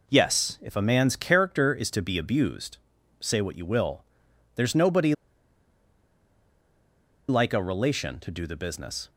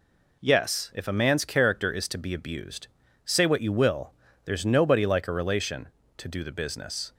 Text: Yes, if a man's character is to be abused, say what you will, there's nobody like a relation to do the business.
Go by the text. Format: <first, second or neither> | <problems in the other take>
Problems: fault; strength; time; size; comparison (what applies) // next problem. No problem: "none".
second | pauses between "nobody" and "like"; strong; at 5.1 s; 2.1 s long